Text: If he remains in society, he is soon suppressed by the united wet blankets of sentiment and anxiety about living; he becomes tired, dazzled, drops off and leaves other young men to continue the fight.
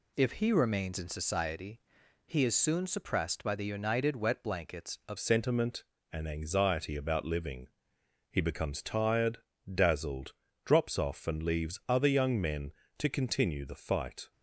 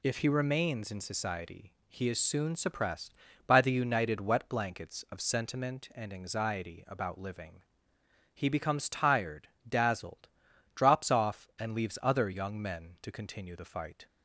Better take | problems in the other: second | changes voice at "sentiment"; from 5.1 s on; 9.2 s long

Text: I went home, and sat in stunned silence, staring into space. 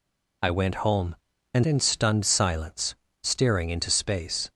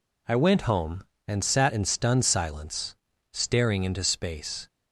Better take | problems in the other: second | skips "sat"; at 1.6 s

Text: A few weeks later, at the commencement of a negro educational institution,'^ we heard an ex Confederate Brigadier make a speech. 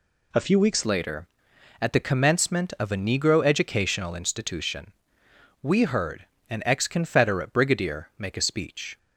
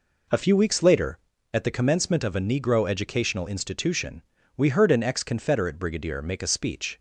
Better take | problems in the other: second | changes voice at "later"; from 0.8 s on; 8.1 s long // pauses between "heard" and "an"; slight; at 6.2 s; 0.26 s long

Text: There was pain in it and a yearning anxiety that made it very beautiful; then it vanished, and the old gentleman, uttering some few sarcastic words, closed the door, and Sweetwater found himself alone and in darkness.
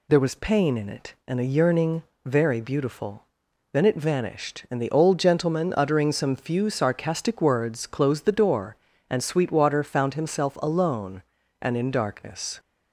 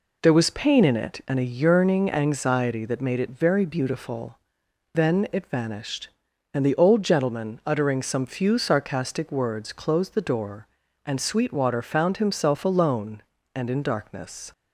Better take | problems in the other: second | skips "anxiety that made it"; at 2.1 s

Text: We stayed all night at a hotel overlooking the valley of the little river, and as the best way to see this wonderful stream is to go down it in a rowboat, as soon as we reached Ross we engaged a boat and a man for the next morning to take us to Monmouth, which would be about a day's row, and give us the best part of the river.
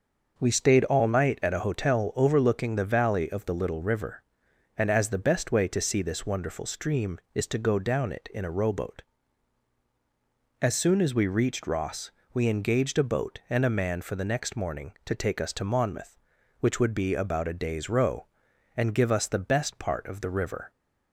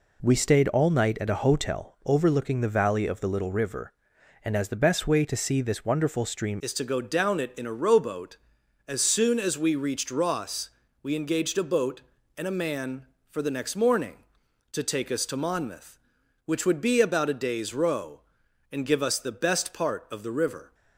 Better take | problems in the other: first | changes voice at "is"; from 6.6 s on; 14.1 s long // pauses between "Ross" and "we"; slight; at 10.6 s; 0.32 s long; slight in the first

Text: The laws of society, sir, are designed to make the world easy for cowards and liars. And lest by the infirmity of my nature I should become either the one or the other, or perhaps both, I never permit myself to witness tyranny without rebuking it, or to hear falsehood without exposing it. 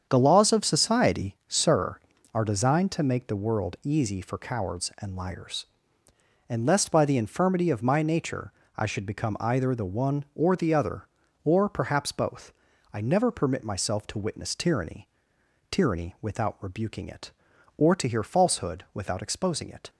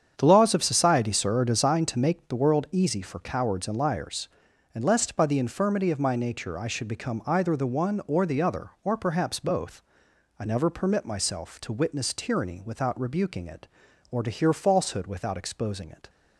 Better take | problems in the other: second | starts louder than the rest; strong; until 1.1 s; 7.5 dB; strong in the second // pauses between "nature" and "I"; slight; at 8.5 s; 0.24 s long // says "tyranny" twice; at 15.6 s

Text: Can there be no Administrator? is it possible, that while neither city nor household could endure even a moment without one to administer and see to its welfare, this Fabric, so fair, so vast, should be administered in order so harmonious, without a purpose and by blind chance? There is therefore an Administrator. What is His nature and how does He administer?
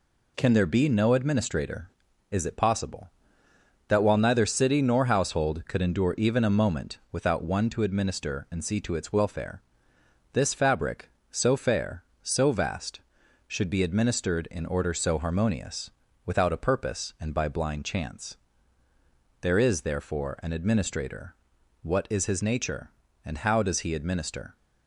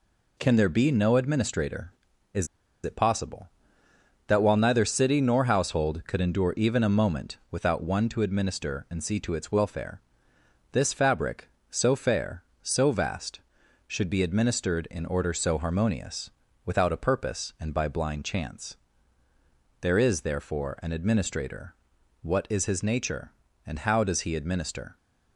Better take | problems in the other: first | pauses between "is" and "it"; at 2.4 s; 0.37 s long

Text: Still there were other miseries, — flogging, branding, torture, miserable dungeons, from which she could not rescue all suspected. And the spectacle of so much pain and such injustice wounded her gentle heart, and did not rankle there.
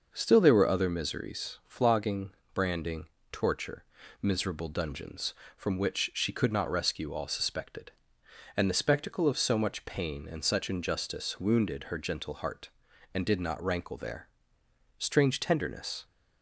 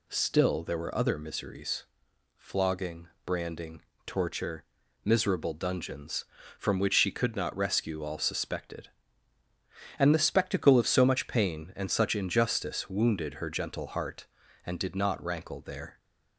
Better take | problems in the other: second | goes on to say "Strange tenderness"; noticeable; from 14.9 s on; 1.0 s long

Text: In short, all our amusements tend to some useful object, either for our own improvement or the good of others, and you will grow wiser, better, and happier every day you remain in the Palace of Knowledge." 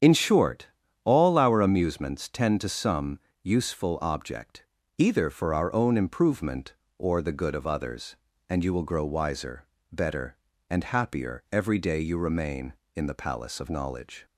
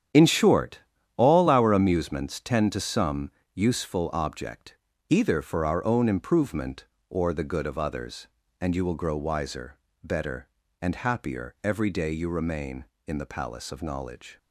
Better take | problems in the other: first | gets quieter; strong; throughout; 11 dB // starts louder than the rest; strong; until 1.5 s; 9.5 dB; strong in the first // pauses between "some" and "useful"; slight; at 3.2 s; 0.24 s long; slight in the first

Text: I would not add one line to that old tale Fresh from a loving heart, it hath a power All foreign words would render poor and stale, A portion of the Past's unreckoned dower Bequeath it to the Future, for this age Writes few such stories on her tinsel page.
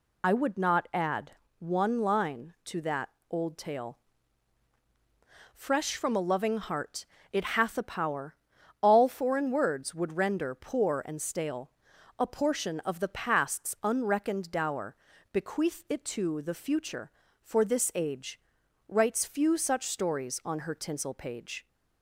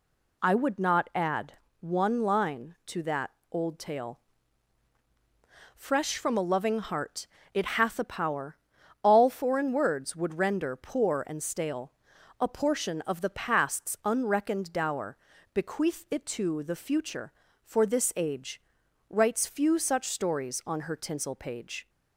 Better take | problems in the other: second | loses the start of "I"; at 0.2 s; 45 ms // pauses between "add" and "one"; slight; at 1.3 s; 0.28 s long; slight in the second // pauses between "that" and "old"; slight; at 3.0 s; 0.20 s long; slight in the second // pauses between "tale" and "Fresh"; strong; at 3.9 s; 1.5 s long; strong in the second // pauses between "power" and "All"; noticeable; at 8.3 s; 0.46 s long; noticeable in the second // pauses between "dower" and "Bequeath"; slight; at 14.9 s; 0.36 s long; slight in the second // pauses between "age" and "Writes"; noticeable; at 18.3 s; 0.48 s long; noticeable in the second

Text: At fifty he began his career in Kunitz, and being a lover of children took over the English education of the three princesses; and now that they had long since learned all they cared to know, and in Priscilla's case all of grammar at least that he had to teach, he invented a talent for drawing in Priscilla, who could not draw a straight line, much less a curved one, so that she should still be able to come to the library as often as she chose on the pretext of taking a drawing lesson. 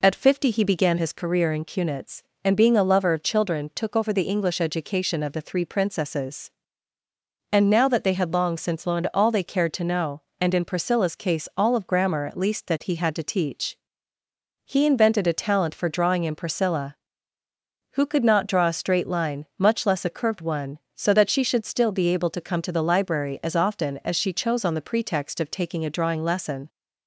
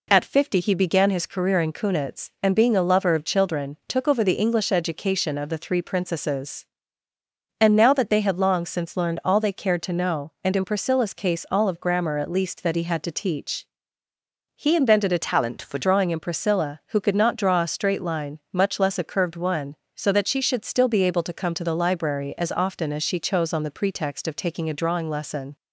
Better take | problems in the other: first | changes voice from "talent" to "for"; from 15.2 to 15.7 s; 0.5 s long

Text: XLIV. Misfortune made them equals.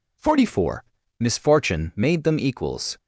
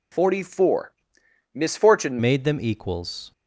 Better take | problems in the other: first | changes voice at "made"; from 2.1 s on; 1.2 s long

